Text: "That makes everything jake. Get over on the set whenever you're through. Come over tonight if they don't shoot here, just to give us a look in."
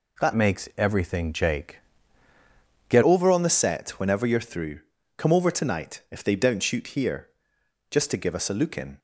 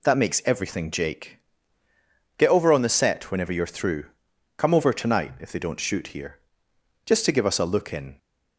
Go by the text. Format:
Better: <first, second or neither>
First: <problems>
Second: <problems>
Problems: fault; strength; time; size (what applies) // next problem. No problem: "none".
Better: second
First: changes voice from "makes" to "Get"; from 0.3 to 3.0 s; 2.7 s long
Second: none